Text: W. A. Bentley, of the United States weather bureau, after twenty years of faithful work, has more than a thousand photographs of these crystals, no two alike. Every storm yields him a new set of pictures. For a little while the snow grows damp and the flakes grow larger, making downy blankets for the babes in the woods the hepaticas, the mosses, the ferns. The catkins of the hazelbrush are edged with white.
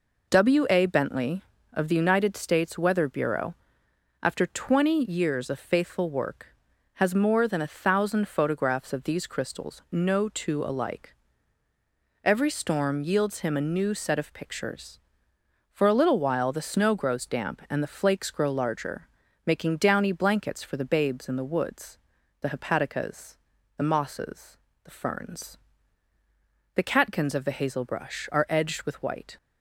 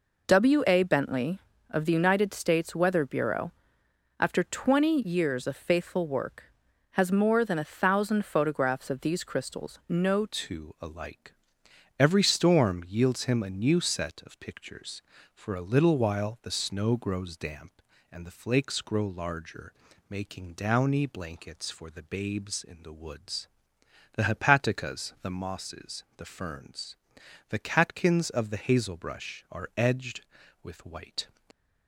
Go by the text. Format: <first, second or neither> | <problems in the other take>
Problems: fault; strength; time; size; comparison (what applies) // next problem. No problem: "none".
first | changes voice at "two"; from 10.2 s on; 21.0 s long // pauses between "woods" and "the"; noticeable; at 23.4 s; 0.66 s long; also in the first